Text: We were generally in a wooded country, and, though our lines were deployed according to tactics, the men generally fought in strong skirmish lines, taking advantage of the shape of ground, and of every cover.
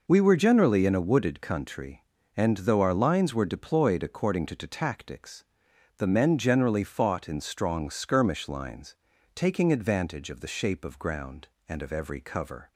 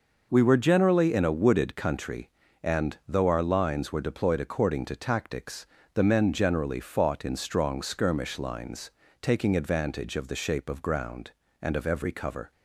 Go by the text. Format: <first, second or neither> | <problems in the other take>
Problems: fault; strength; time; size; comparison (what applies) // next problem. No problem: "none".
second | says "to" twice; at 4.5 s